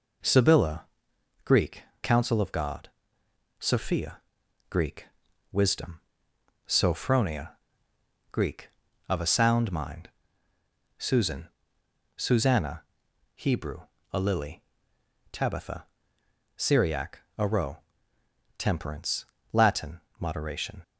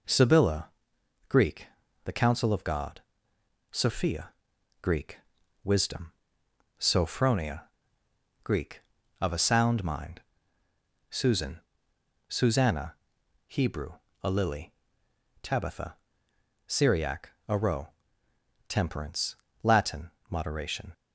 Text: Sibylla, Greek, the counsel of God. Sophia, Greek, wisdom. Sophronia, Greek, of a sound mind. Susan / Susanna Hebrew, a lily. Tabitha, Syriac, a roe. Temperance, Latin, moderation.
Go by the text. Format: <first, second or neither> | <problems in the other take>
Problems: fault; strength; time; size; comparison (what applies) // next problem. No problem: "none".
second | skips "the"; at 1.9 s // pauses between "Susanna" and "Hebrew"; noticeable; at 12.8 s; 0.54 s long; noticeable in the second